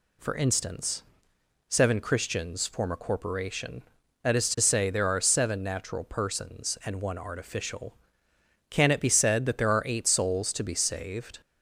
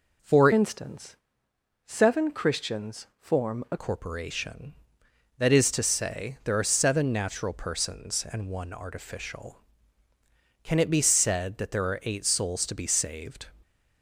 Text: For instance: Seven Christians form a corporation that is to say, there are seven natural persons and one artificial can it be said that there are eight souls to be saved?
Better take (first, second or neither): first